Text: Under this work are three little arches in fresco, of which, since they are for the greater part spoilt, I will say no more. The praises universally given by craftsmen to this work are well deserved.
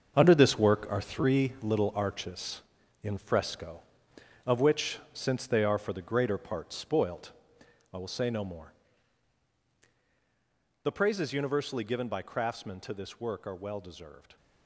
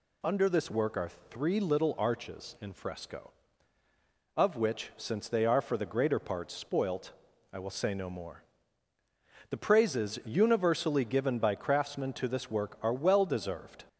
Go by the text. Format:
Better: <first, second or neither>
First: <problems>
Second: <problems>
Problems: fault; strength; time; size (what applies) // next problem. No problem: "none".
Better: second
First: gets quieter; strong; throughout; 10 dB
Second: none